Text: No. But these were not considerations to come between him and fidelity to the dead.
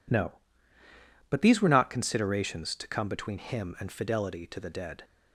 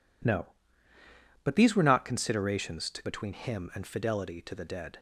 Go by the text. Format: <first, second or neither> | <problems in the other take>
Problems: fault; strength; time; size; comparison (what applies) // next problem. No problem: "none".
first | skips "come"; at 3.0 s